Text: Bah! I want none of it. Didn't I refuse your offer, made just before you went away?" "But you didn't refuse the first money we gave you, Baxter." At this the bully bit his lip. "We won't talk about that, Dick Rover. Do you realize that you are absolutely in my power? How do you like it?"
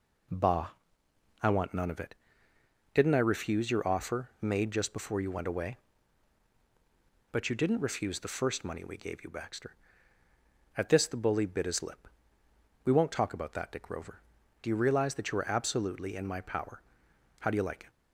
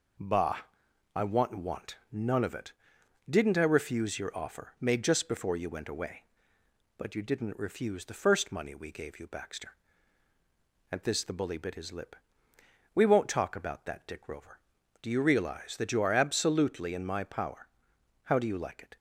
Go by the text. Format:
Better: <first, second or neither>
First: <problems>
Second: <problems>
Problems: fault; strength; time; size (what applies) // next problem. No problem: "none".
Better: first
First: none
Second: says "want" twice; at 1.5 s